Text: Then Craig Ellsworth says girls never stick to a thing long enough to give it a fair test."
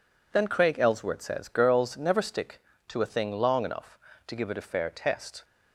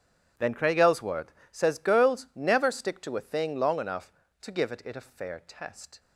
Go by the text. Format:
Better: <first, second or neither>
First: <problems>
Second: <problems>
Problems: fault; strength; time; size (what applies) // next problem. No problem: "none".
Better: first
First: none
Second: pauses between "Ellsworth" and "says"; slight; at 1.3 s; 0.20 s long // says "it" twice; at 4.8 s